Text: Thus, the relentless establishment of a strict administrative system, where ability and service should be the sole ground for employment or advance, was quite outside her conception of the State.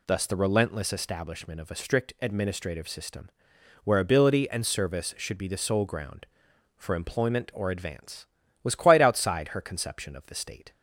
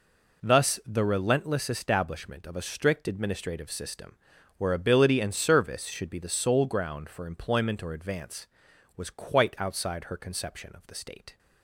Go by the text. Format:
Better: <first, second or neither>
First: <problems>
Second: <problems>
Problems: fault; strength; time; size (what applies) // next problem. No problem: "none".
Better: neither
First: none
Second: none